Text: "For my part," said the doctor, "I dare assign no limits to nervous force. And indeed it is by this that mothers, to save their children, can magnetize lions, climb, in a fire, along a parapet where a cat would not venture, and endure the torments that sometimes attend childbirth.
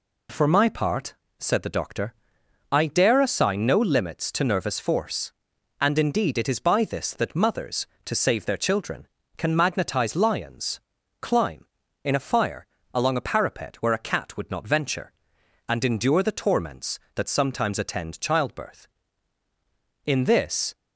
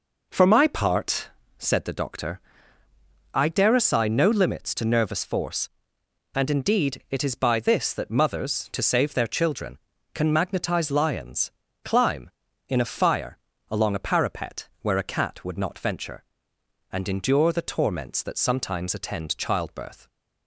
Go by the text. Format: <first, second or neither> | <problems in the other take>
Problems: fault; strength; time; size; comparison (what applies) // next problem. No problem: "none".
second | goes on to say "In this"; noticeable; from 20.0 s on; 0.68 s long